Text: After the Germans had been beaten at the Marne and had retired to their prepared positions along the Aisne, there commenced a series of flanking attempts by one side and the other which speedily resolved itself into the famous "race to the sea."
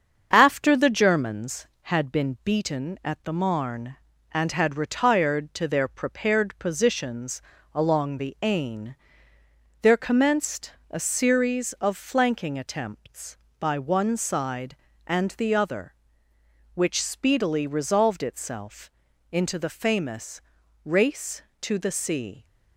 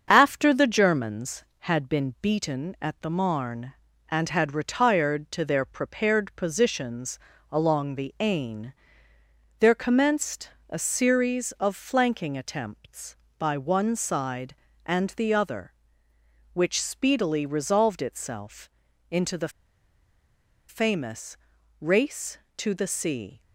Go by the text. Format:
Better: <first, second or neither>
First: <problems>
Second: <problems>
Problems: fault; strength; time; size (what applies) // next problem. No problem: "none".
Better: first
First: starts louder than the rest; strong; until 1.3 s; 7 dB // pauses between "positions" and "along"; slight; at 7.4 s; 0.32 s long // pauses between "commenced" and "a"; slight; at 10.7 s; 0.16 s long // pauses between "itself" and "into"; at 18.8 s; 0.44 s long // pauses between "famous" and "race"; at 20.3 s; 0.44 s long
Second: starts louder than the rest; strong; until 1.0 s; 7 dB // pauses between "positions" and "along"; slight; at 7.1 s; 0.32 s long // pauses between "commenced" and "a"; slight; at 10.4 s; 0.18 s long // pauses between "itself" and "into"; at 18.6 s; 0.44 s long // pauses between "the" and "famous"; at 19.4 s; 1.1 s long // pauses between "famous" and "race"; at 21.3 s; 0.44 s long